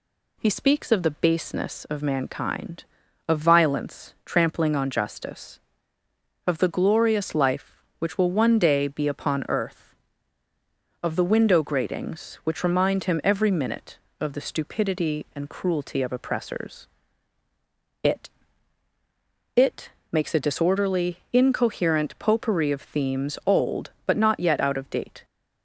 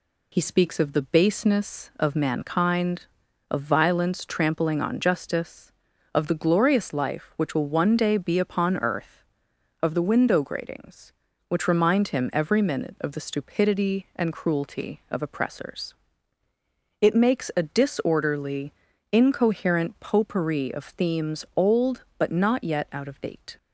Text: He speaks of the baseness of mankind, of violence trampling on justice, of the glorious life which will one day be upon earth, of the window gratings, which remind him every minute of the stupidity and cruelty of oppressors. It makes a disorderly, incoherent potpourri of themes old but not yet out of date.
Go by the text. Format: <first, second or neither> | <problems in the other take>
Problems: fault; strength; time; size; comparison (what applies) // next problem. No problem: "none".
second | says "It" twice; at 19.5 s